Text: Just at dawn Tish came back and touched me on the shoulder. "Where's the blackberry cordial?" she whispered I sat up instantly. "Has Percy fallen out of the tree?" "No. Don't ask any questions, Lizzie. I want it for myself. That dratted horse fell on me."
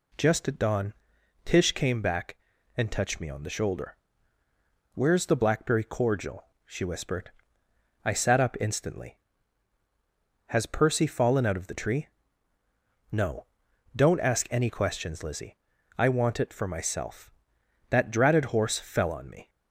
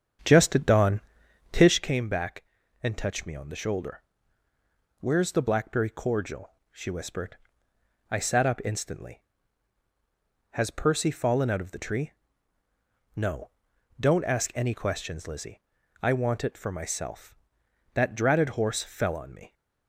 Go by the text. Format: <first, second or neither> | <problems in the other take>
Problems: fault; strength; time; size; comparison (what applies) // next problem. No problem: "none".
first | starts louder than the rest; strong; until 1.8 s; 8 dB // pauses between "dawn" and "Tish"; noticeable; at 1.0 s; 0.50 s long; noticeable in the first // pauses between "whispered" and "I"; noticeable; at 7.3 s; 0.74 s long; noticeable in the first